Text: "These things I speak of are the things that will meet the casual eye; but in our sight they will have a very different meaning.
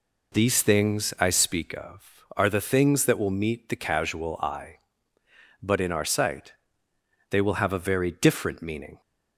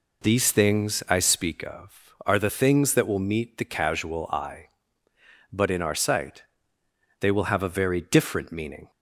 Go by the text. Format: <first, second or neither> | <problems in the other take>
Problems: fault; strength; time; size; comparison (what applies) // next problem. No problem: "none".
neither | pauses between "sight" and "they"; noticeable; the same in both